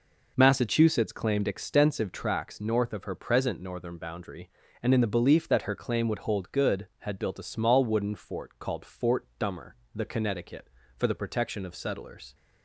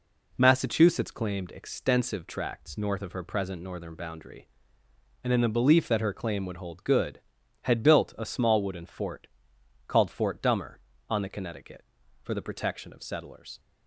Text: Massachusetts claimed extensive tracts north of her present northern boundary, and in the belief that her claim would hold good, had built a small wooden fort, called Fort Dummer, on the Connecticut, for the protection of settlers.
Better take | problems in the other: second | skips "on"; at 9.8 s

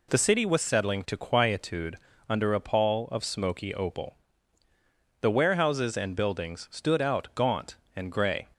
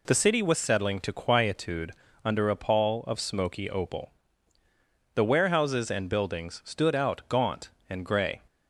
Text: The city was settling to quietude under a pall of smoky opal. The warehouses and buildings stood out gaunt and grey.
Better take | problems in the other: neither | pauses between "quietude" and "under"; slight; the same in both

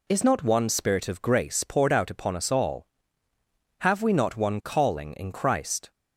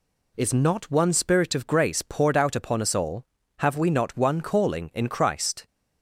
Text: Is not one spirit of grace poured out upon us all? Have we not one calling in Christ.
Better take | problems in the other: neither | none

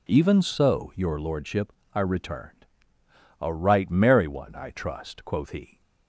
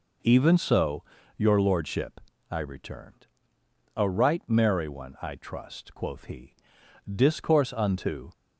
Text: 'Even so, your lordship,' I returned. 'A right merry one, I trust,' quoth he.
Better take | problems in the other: first | goes on to say "Discourse unto"; noticeable; from 7.0 s on; 1.2 s long

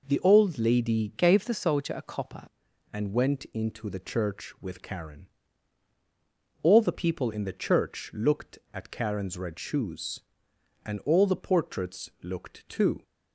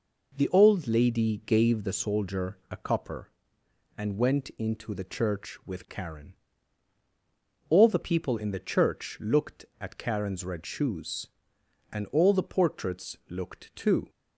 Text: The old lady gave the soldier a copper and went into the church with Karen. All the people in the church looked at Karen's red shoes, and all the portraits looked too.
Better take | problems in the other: second | changes voice from "gave" to "copper"; from 1.1 to 2.4 s; 1.3 s long

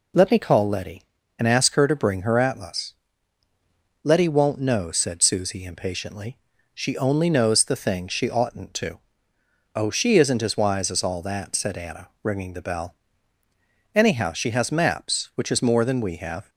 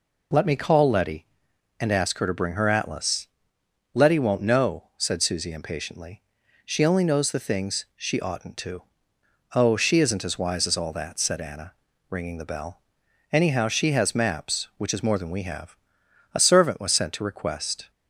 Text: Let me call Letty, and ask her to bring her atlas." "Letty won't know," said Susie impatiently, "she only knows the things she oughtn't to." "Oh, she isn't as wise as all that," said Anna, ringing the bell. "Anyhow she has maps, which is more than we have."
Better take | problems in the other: first | goes on to say "A servant was sent to request"; from 16.3 s on; 1.5 s long

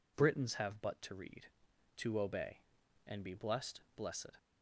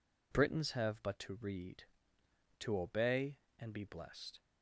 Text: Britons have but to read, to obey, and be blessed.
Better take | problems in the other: second | says "blessed" twice; at 3.9 s

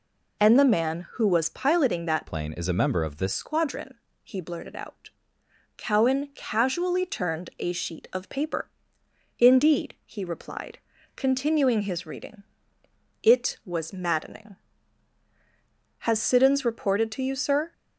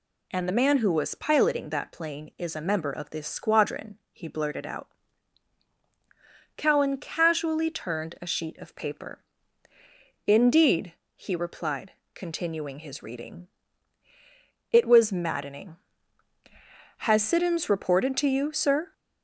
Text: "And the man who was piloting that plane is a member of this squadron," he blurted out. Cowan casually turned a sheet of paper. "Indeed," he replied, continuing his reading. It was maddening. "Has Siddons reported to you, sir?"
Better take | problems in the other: second | changes voice from "plane" to "this"; from 2.2 to 3.3 s; 1.1 s long

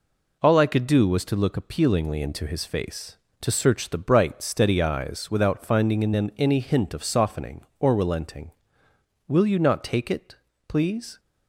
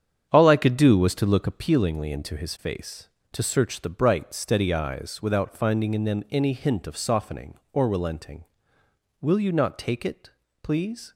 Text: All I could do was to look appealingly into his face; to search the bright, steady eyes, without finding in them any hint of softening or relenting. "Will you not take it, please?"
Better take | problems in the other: first | starts louder than the rest; strong; until 1.9 s; 8 dB

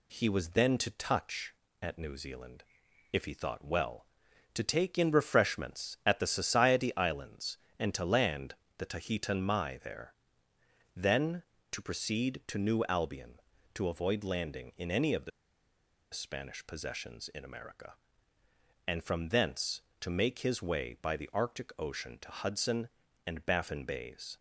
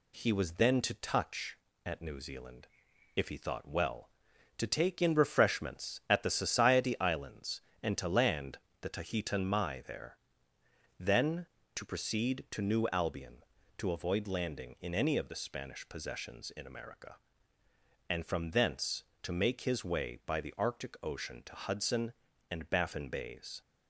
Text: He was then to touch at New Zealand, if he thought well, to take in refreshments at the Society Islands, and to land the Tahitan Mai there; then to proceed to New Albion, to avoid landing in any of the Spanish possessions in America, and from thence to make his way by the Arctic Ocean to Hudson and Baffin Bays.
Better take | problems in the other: second | pauses between "land" and "the"; slight; at 8.5 s; 0.22 s long; slight in the second // pauses between "the" and "Spanish"; noticeable; at 15.3 s; 0.81 s long

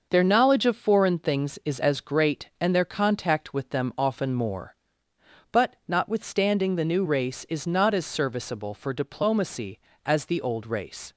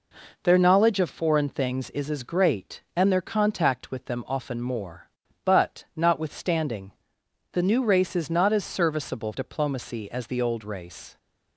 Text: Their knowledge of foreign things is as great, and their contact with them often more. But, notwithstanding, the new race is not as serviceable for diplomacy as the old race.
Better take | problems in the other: first | skips "for"; at 9.3 s

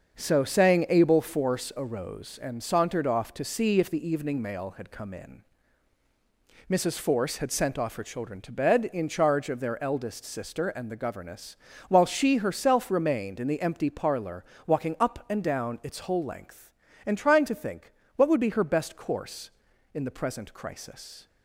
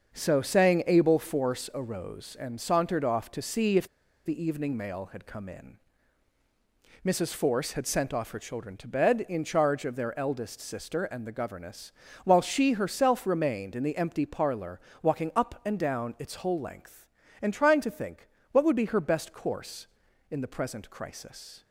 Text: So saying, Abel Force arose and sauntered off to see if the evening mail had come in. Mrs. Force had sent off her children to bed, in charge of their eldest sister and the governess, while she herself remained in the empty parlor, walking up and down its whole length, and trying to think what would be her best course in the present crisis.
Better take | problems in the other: first | starts louder than the rest; until 1.1 s; 6.5 dB; also in the first // pauses between "if" and "the"; at 3.8 s; 0.37 s long // pauses between "think" and "what"; slight; at 18.2 s; 0.24 s long; slight in the first

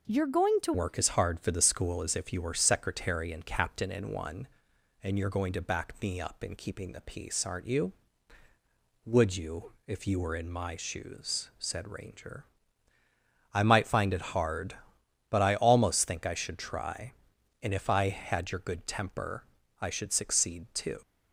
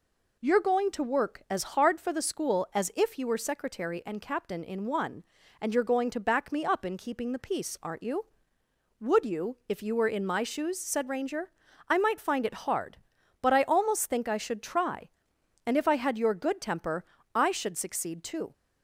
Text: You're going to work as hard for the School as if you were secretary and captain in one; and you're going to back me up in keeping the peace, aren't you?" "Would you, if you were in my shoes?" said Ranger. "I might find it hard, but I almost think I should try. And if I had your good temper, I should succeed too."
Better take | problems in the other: second | changes voice at "work"; from 0.7 s on; 20.3 s long

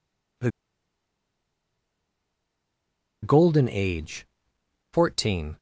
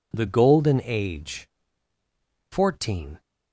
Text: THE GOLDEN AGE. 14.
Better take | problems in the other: second | pauses between "THE" and "GOLDEN"; strong; at 0.5 s; 2.7 s long

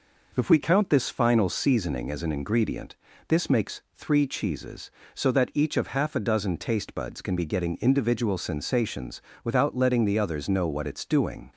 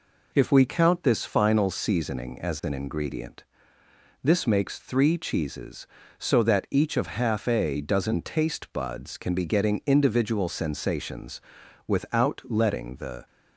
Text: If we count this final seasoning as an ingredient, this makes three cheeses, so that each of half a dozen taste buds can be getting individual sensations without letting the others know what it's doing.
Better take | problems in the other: first | pauses between "sensations" and "without"; noticeable; at 11.3 s; 0.48 s long; slight in the first // stops before "others know what it's doing"; at 13.2 s

